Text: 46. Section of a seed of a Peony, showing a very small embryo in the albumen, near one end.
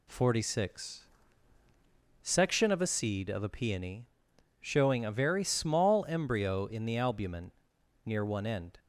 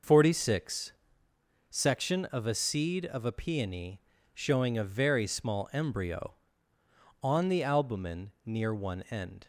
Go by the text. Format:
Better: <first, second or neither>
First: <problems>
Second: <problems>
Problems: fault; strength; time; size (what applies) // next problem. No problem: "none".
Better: first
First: none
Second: says "on" for "in"; at 7.2 s